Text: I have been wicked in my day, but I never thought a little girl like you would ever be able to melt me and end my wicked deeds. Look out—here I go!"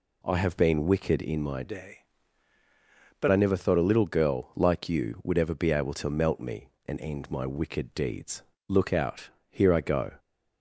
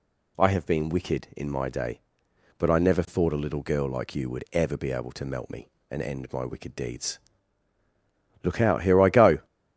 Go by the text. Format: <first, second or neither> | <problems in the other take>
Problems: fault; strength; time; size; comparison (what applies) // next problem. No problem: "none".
second | changes voice from "day" to "but"; from 1.6 to 3.2 s; 1.6 s long